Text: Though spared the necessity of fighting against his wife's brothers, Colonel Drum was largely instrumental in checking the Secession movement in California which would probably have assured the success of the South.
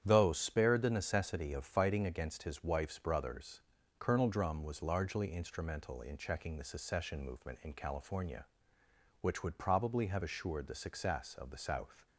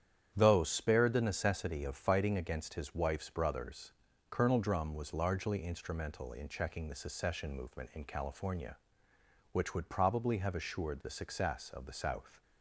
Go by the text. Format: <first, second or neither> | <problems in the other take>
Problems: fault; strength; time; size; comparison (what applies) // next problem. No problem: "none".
neither | starts louder than the rest; strong; the same in both